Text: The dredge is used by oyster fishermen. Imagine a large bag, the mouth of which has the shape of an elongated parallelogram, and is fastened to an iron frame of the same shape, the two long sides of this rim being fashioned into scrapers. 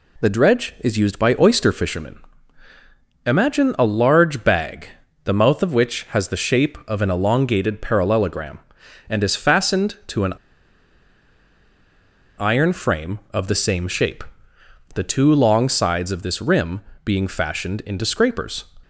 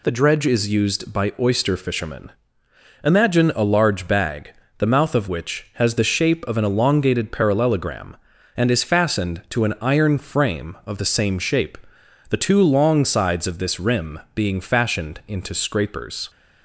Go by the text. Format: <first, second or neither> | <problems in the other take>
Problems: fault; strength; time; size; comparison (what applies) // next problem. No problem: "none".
second | pauses between "an" and "iron"; strong; at 10.3 s; 2.0 s long // pauses between "rim" and "being"; slight; at 16.8 s; 0.24 s long; slight in the second